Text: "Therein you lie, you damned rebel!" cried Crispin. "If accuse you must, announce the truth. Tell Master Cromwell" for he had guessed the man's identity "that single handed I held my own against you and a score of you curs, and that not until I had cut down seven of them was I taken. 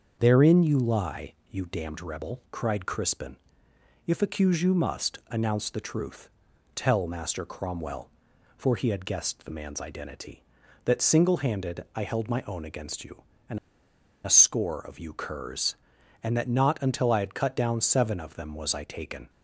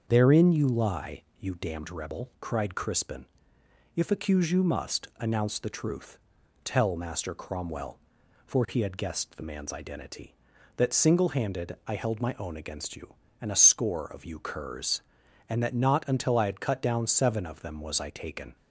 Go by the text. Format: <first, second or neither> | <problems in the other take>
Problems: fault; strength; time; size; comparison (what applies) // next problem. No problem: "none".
second | starts louder than the rest; until 1.2 s; 6.5 dB; also in the second // pauses between "and" and "a"; noticeable; at 13.5 s; 0.67 s long